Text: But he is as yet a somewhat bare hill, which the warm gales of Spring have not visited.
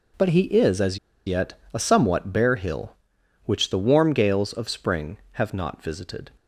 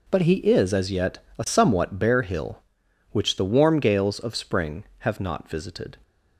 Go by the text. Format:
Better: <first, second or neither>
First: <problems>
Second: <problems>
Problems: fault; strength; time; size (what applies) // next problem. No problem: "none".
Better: second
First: pauses between "as" and "yet"; slight; at 0.9 s; 0.29 s long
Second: none